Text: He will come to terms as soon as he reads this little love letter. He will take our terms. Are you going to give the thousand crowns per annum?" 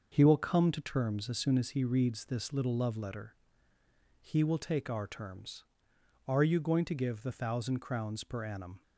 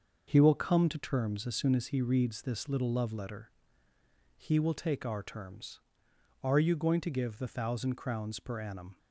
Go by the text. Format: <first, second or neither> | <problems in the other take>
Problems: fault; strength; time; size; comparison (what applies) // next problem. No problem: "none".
neither | starts louder than the rest; the same in both